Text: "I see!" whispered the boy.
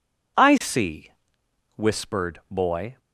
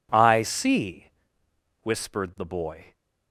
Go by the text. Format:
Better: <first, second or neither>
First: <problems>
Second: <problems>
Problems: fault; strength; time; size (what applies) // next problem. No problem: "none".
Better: second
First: skips "the"; at 2.4 s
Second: none